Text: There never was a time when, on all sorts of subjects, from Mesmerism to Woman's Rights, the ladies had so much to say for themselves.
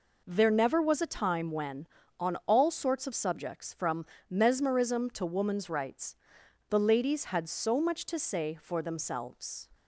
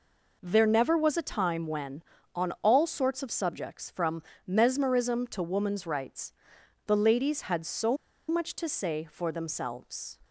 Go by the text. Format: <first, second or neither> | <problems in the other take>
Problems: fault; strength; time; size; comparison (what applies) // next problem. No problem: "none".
first | pauses between "from" and "Mesmerism"; slight; at 4.2 s; 0.24 s long; slight in the first // pauses between "so" and "much"; slight; at 7.9 s; 0.32 s long